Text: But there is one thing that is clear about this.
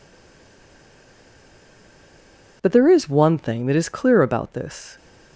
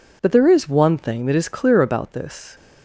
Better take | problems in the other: second | stays silent before the first word; strong; until 2.6 s; 2.6 s long

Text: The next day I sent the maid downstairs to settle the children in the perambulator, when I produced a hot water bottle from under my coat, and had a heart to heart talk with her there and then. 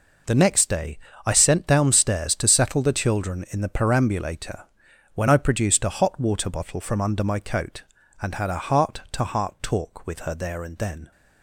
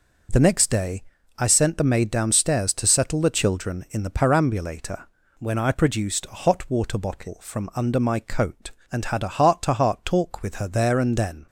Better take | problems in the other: second | pauses between "day" and "I"; slight; at 0.9 s; 0.28 s long; also in the second // skips "the maid"; at 1.6 s

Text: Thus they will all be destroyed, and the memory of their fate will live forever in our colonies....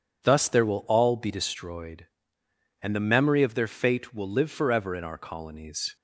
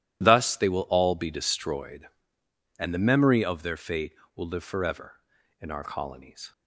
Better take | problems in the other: second | says "there" for "they"; at 0.4 s

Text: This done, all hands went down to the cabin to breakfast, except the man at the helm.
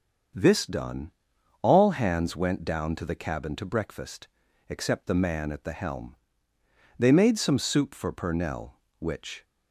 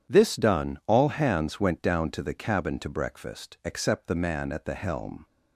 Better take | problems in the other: second | starts louder than the rest; until 1.8 s; 7 dB // goes on to say "They made some soup for Purnell which"; strong; from 6.9 s on; 2.4 s long

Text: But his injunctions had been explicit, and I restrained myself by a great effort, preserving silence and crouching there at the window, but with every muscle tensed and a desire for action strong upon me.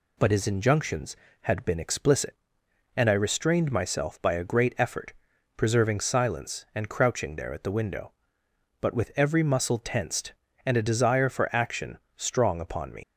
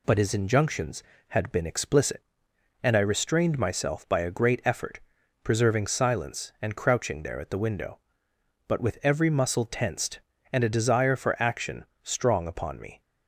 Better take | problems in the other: second | pauses between "action" and "strong"; slight; at 11.9 s; 0.16 s long; slight in the second // leaves "me" unfinished; at 13.0 s; 100 ms

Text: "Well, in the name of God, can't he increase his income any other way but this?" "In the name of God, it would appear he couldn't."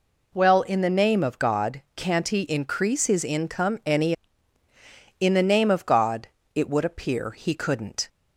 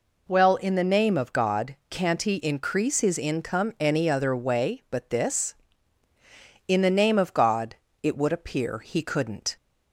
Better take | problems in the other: second | skips "other way but this"; at 4.6 s

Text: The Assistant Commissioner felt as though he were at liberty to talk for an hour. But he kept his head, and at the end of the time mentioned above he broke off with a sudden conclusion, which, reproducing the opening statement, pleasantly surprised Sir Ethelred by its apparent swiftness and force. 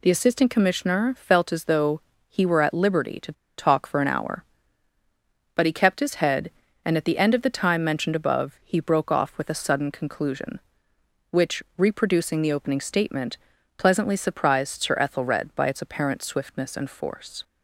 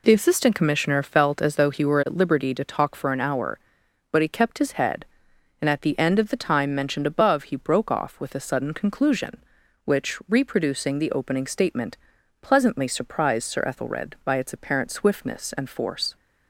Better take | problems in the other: second | pauses between "though" and "he"; slight; at 2.0 s; 0.26 s long // pauses between "to" and "talk"; slight; at 3.3 s; 0.25 s long

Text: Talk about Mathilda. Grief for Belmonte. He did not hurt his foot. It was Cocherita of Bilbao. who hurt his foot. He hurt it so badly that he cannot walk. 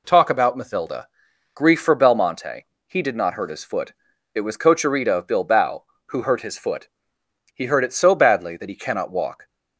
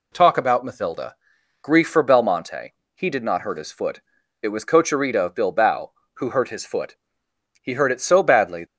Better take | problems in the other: first | stops before "that he cannot walk"; at 8.6 s

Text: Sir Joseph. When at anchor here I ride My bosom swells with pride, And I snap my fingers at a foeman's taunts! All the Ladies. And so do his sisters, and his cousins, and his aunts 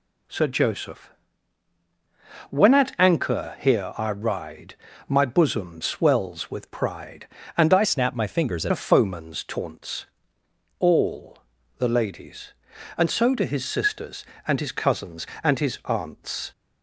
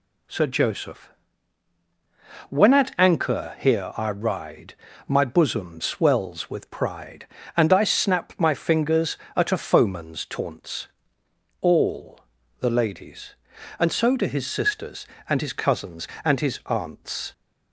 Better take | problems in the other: second | pauses between "ride" and "My"; slight; at 4.7 s; 0.34 s long; slight in the second // changes voice from "snap" to "at"; from 7.8 to 8.7 s; 0.9 s long // pauses between "All" and "the"; at 11.3 s; 0.40 s long; also in the second

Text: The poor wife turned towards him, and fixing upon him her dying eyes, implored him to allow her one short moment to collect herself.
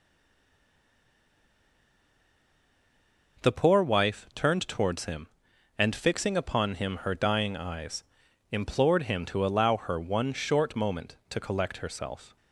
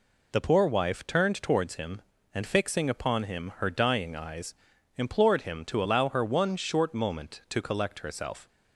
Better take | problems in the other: second | stays silent before the first word; strong; until 3.3 s; 3.3 s long

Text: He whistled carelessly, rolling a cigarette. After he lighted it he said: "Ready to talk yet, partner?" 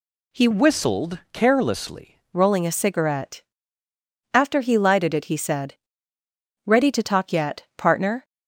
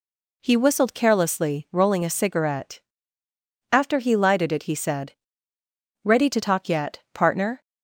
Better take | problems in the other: second | changes voice from "whistled" to "carelessly"; from 0.5 to 2.1 s; 1.6 s long

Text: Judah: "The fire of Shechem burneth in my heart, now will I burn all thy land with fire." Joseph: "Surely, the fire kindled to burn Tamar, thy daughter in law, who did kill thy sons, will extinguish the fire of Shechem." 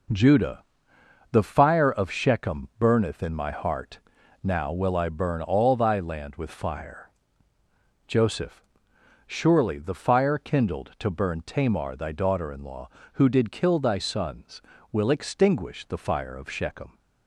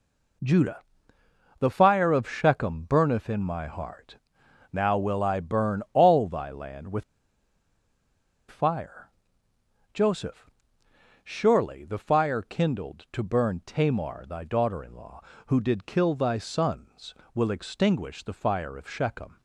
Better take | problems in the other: first | pauses between "with" and "fire"; strong; at 7.0 s; 1.4 s long

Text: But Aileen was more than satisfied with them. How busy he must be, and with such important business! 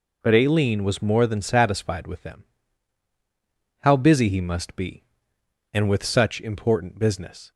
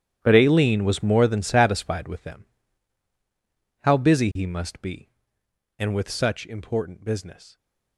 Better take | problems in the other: first | gets quieter; strong; throughout; 16.5 dB

